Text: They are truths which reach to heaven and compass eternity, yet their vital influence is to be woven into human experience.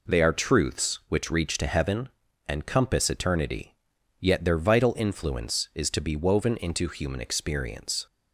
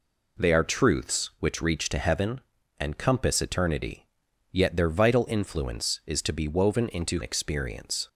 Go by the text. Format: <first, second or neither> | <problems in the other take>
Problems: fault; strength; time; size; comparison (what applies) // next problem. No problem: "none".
first | skips "human"; at 7.2 s